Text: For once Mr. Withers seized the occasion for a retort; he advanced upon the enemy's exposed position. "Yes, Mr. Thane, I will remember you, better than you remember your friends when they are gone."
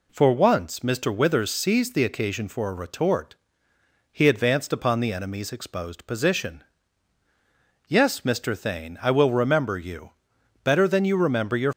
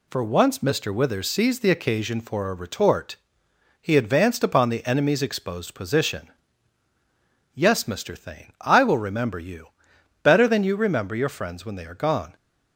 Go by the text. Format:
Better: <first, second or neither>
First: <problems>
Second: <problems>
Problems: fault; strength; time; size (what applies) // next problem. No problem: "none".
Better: second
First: stops before "friends when they are gone"; at 11.7 s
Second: none